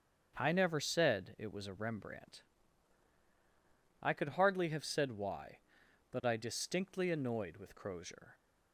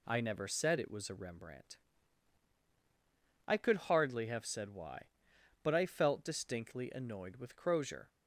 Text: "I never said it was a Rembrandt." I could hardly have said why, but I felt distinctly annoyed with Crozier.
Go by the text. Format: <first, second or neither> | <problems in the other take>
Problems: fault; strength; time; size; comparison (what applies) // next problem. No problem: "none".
second | starts louder than the rest; strong; until 1.4 s; 7.5 dB // skips "felt"; at 6.3 s